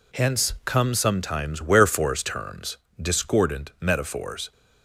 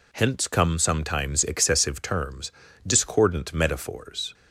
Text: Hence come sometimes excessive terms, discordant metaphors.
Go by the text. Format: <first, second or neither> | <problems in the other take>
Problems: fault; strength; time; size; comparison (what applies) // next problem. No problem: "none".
second | says "wherefores" for "excessive"; at 1.6 s